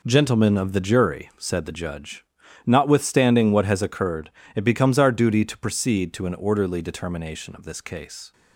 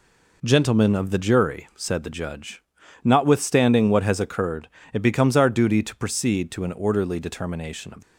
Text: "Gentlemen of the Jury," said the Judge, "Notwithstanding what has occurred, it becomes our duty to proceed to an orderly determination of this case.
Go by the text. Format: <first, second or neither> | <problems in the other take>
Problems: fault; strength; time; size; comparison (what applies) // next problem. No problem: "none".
first | stops before "this case"; at 8.0 s